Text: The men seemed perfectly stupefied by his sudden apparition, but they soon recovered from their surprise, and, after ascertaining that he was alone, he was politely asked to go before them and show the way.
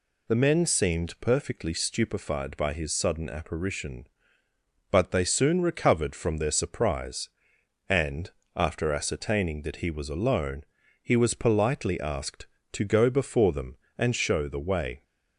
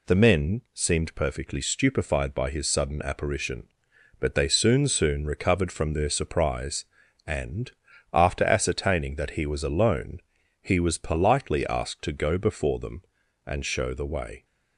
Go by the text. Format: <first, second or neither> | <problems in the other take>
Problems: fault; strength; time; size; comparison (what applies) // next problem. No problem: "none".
first | says "soon" twice; at 4.8 s